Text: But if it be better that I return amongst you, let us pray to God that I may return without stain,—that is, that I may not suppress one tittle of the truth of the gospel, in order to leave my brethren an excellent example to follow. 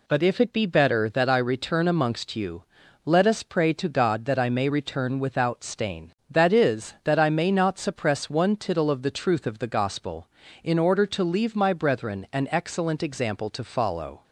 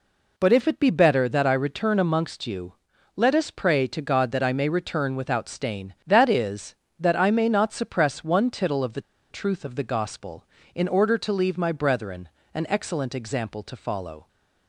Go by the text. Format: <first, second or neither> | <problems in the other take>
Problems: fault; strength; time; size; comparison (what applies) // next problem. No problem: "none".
first | pauses between "the" and "truth"; slight; at 9.0 s; 0.30 s long // pauses between "brethren" and "an"; slight; at 12.2 s; 0.24 s long